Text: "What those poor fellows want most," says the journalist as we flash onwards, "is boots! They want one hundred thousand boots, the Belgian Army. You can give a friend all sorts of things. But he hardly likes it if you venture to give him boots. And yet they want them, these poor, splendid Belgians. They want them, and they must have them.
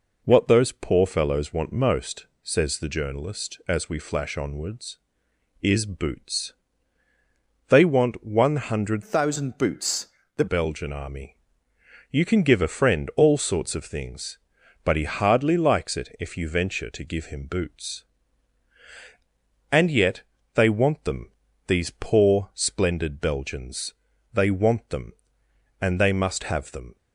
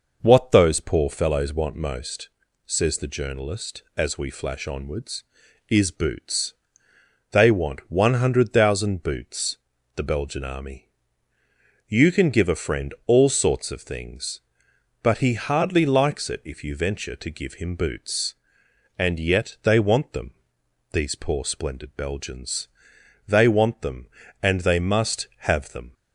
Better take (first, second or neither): second